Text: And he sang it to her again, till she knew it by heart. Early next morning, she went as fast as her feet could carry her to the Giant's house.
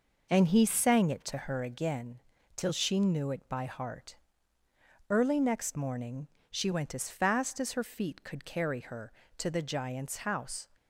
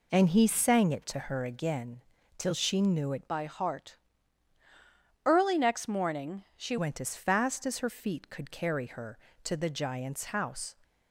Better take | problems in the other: first | changes voice from "by" to "she"; from 3.2 to 6.7 s; 3.5 s long

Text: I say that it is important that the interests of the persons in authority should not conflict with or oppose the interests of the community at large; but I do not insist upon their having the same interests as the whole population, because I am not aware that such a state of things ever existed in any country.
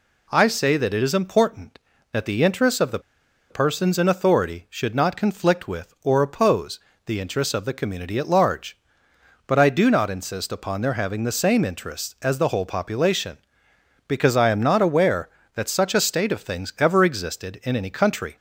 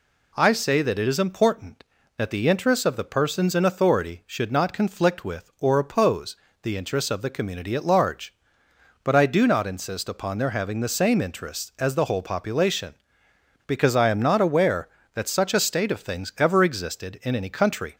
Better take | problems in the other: second | pauses between "the" and "persons"; noticeable; at 2.9 s; 0.50 s long // pauses between "oppose" and "the"; slight; at 6.7 s; 0.26 s long; slight in the second

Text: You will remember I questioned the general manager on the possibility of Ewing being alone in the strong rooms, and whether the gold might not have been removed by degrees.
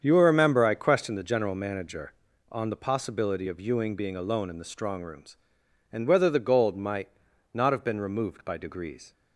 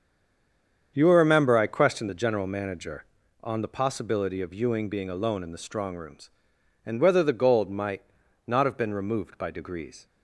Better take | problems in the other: first | stays silent before the first word; slight; until 0.9 s; 0.9 s long // starts louder than the rest; strong; until 1.9 s; 7.5 dB; strong in the first // pauses between "might" and "not"; at 8.0 s; 0.42 s long; also in the first

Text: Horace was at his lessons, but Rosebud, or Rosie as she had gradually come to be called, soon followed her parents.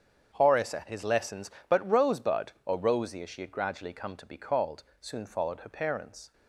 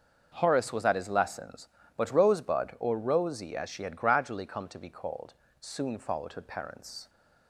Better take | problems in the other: second | starts louder than the rest; strong; until 1.3 s; 8 dB; also in the second // skips "was"; at 0.7 s

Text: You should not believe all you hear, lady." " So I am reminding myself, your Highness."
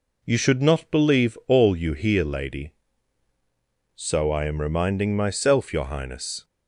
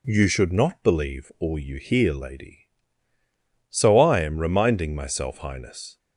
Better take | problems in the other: first | skips "your"; at 5.3 s

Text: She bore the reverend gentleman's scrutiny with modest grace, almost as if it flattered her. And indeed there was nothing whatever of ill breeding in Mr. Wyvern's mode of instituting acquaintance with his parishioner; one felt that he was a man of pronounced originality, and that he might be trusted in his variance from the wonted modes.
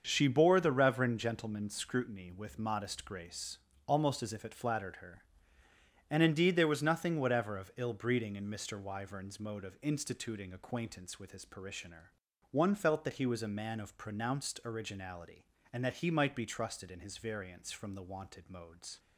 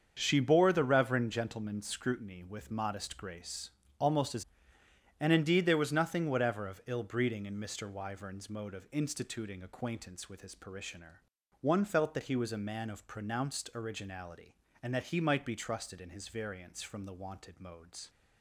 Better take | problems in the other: first | starts louder than the rest; until 1.2 s; 7 dB; also in the first // skips "if it flattered her"; at 4.8 s

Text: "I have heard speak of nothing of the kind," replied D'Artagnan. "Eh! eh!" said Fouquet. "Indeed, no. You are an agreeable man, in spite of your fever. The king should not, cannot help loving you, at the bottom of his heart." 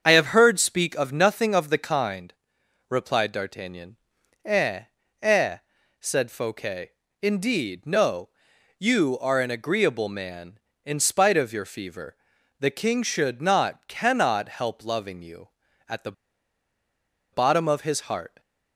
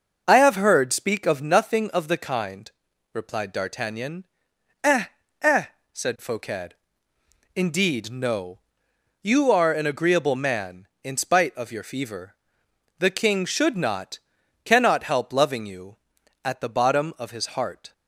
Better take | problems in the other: second | starts louder than the rest; strong; until 1.0 s; 7.5 dB // pauses between "the" and "bottom"; at 16.1 s; 1.2 s long

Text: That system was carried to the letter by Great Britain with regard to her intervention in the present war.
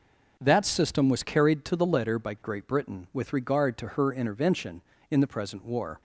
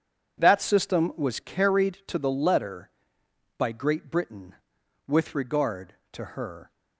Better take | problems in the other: first | stops before "intervention in the present war"; at 6.7 s

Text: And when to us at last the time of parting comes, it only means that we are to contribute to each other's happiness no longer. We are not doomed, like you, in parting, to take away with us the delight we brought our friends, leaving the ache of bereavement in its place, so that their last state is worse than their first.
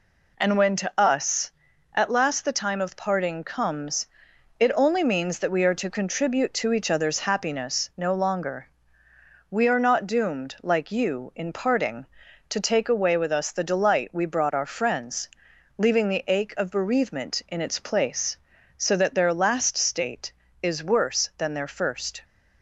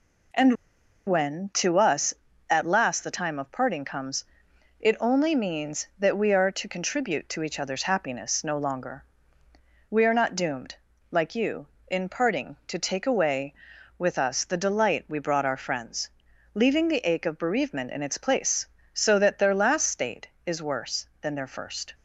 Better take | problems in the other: first | pauses between "And" and "when"; noticeable; at 0.5 s; 0.52 s long

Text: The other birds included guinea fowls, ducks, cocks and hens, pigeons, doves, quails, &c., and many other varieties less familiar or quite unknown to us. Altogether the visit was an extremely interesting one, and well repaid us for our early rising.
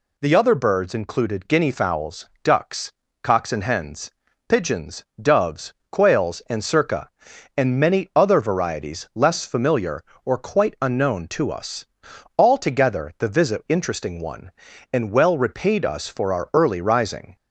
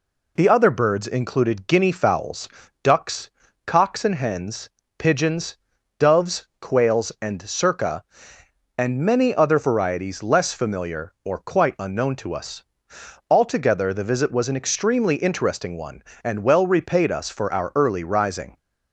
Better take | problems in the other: second | skips "was an extremely"; at 13.6 s

